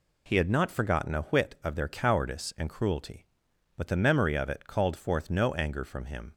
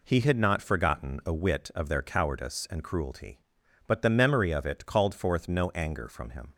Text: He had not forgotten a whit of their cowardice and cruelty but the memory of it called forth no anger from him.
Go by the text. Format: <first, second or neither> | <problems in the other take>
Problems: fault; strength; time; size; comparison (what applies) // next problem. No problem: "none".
neither | none